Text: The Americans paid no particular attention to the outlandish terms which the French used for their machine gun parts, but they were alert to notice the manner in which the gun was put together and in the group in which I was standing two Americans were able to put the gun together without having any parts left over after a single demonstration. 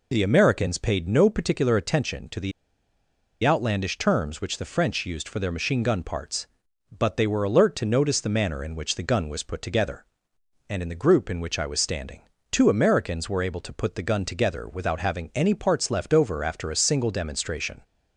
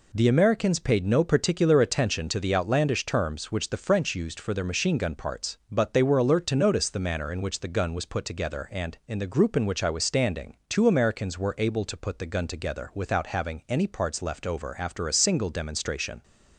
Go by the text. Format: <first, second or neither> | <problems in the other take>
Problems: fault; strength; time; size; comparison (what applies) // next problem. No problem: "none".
second | pauses between "the" and "outlandish"; noticeable; at 2.5 s; 0.92 s long // pauses between "standing" and "two"; slight; at 12.2 s; 0.30 s long